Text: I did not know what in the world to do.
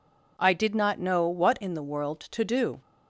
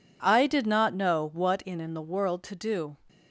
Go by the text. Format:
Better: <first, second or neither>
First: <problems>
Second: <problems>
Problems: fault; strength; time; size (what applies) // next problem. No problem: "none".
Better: first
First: none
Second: says "in" twice; at 1.8 s